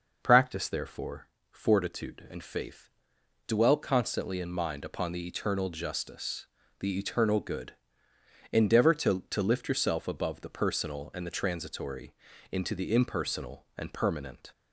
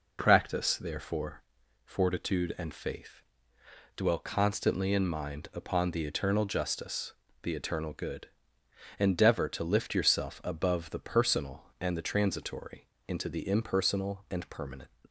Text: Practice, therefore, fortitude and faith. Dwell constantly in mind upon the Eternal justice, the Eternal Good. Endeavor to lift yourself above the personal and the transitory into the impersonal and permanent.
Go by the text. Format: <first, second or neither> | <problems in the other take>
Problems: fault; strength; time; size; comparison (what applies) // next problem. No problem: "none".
second | says "to" twice; at 9.2 s // pauses between "transitory" and "into"; at 12.1 s; 0.38 s long; slight in the second